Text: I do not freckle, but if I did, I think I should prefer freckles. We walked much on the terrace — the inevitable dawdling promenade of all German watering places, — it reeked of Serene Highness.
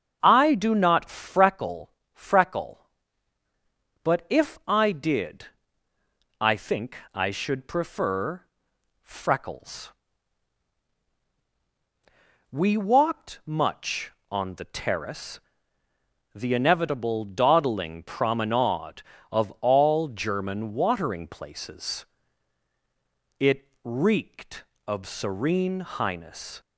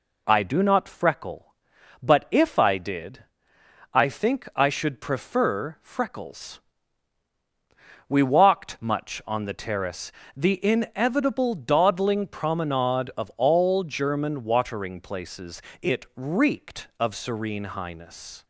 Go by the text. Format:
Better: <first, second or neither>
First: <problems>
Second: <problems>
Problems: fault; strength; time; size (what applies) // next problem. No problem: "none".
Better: second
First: starts louder than the rest; until 1.2 s; 7 dB // says "freckle" twice; at 2.1 s // pauses between "think" and "I"; slight; at 6.9 s; 0.18 s long // pauses between "prefer" and "freckles"; noticeable; at 8.4 s; 0.60 s long // pauses between "it" and "reeked"; slight; at 23.6 s; 0.16 s long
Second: none